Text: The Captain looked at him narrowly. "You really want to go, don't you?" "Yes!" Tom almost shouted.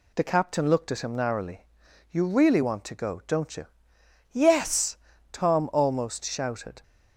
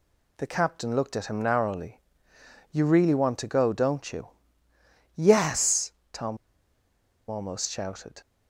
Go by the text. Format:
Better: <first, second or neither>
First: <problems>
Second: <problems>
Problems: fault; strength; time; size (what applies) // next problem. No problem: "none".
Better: first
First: none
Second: pauses between "Tom" and "almost"; noticeable; at 6.3 s; 0.93 s long